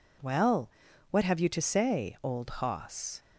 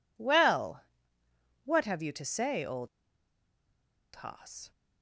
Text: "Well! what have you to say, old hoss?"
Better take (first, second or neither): first